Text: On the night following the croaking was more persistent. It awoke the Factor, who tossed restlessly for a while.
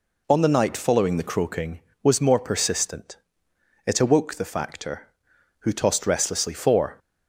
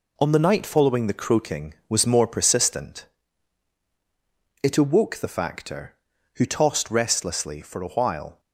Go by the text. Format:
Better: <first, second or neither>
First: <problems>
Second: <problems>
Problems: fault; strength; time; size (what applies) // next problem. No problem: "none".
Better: second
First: stops before "a while"; at 6.9 s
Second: none